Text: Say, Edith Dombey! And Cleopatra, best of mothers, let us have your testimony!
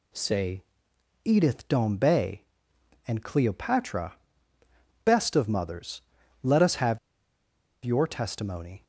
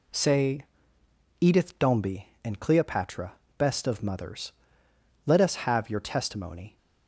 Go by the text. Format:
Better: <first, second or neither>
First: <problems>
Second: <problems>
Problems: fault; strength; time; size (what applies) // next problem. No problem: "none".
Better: second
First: pauses between "have" and "your"; noticeable; at 6.9 s; 0.86 s long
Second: none